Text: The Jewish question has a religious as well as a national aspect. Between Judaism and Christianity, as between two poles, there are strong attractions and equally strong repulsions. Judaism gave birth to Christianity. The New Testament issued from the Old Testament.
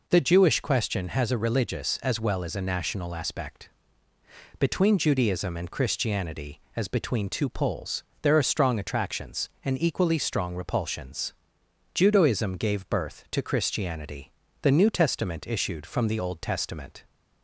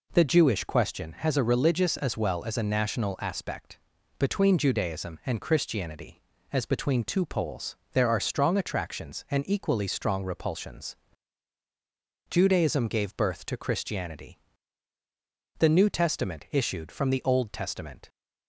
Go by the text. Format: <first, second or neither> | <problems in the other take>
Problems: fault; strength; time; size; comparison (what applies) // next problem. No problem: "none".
neither | none